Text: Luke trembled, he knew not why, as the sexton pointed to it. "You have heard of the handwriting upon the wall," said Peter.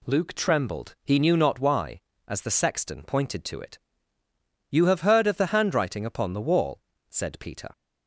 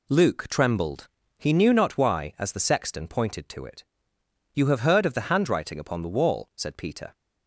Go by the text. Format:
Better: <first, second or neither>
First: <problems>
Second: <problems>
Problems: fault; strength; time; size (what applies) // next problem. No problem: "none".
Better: neither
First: none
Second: none